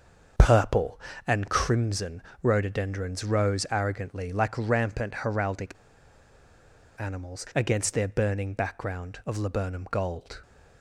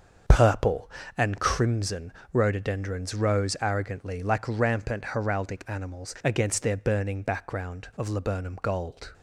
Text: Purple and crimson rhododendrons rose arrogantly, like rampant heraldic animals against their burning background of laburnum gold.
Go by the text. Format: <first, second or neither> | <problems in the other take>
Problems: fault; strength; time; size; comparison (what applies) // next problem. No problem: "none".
second | starts louder than the rest; until 1.6 s; 6.5 dB; also in the second // pauses between "crimson" and "rhododendrons"; slight; at 2.2 s; 0.22 s long; slight in the second // pauses between "heraldic" and "animals"; strong; at 5.7 s; 1.2 s long